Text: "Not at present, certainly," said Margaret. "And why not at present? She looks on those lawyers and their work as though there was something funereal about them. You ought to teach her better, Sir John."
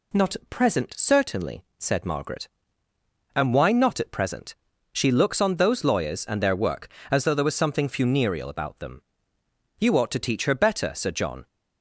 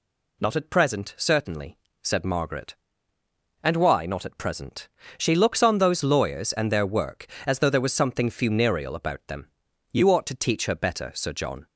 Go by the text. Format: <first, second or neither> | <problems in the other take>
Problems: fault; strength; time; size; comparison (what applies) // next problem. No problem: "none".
neither | none